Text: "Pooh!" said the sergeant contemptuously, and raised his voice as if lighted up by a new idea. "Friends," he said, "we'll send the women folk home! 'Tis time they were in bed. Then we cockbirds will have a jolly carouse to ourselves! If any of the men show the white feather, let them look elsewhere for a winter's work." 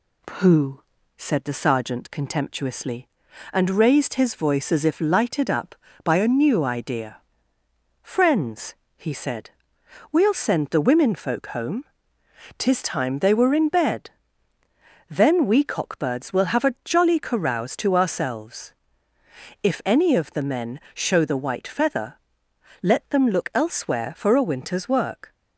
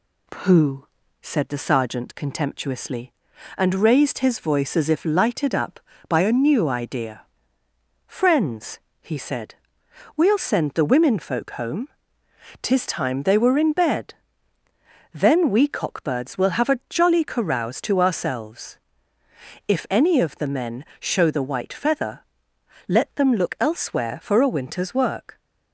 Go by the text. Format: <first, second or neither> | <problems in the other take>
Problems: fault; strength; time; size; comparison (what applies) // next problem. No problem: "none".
neither | none